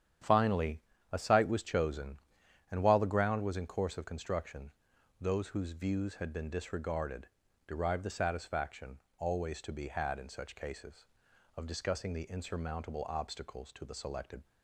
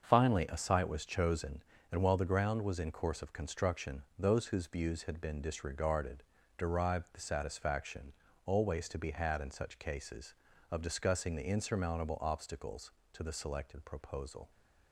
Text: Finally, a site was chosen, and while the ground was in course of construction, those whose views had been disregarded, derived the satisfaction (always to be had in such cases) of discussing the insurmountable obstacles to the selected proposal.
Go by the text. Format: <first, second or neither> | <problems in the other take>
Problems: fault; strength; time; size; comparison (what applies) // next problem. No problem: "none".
second | starts louder than the rest; strong; until 1.5 s; 9.5 dB; also in the second // stops before "proposal"; at 14.4 s